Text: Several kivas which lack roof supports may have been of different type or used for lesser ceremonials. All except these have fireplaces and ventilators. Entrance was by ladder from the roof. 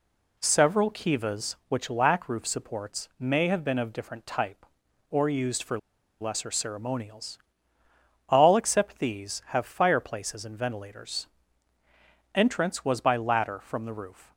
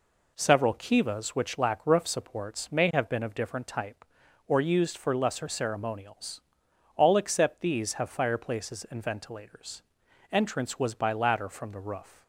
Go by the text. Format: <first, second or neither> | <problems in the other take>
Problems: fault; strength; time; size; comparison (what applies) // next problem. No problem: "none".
second | pauses between "for" and "lesser"; at 5.7 s; 0.41 s long